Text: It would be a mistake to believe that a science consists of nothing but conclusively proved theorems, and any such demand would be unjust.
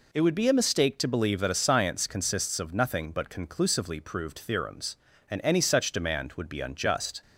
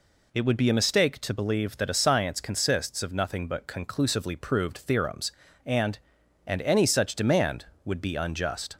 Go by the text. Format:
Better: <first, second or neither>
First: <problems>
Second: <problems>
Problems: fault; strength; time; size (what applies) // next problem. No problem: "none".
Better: first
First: none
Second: says "and" twice; at 6.4 s